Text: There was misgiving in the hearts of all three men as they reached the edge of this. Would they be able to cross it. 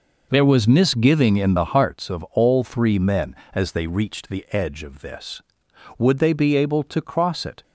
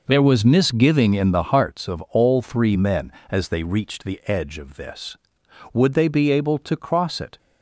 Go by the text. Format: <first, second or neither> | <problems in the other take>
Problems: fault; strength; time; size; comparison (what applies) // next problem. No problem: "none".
neither | none